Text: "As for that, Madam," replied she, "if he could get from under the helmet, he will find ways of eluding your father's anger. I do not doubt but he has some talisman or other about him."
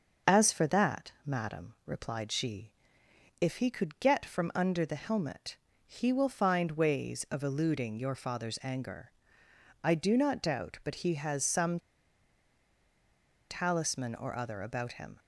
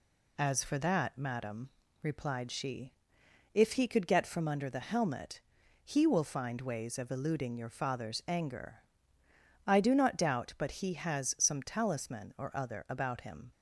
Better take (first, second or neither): second